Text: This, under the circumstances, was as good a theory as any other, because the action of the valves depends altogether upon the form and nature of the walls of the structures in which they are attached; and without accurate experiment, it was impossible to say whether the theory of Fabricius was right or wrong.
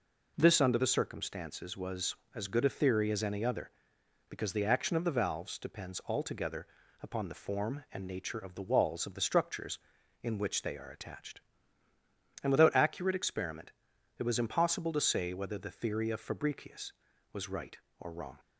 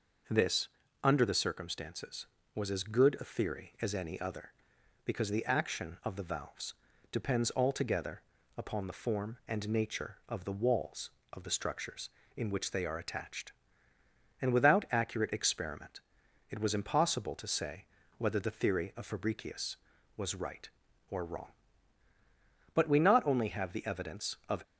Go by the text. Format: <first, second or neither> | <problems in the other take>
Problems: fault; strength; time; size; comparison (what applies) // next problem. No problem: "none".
first | pauses between "valves" and "depends"; at 6.7 s; 0.38 s long // pauses between "altogether" and "upon"; slight; at 8.2 s; 0.34 s long; slight in the first // pauses between "say" and "whether"; slight; at 17.8 s; 0.34 s long // goes on to say "But we not only have the evidence of"; strong; from 22.7 s on; 1.8 s long